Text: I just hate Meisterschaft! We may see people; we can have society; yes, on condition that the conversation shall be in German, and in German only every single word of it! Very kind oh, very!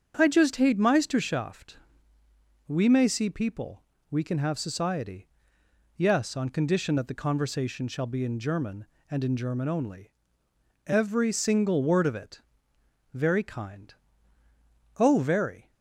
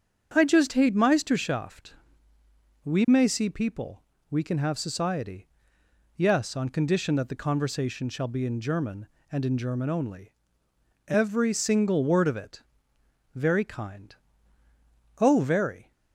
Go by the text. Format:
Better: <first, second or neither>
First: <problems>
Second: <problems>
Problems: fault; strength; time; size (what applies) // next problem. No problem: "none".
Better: neither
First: starts louder than the rest; strong; until 1.1 s; 7.5 dB // pauses between "only" and "every"; noticeable; at 10.1 s; 0.74 s long // pauses between "kind" and "oh"; at 13.9 s; 1.0 s long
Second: starts louder than the rest; strong; until 1.3 s; 7 dB // pauses between "only" and "every"; noticeable; at 10.3 s; 0.74 s long // pauses between "kind" and "oh"; at 14.1 s; 1.0 s long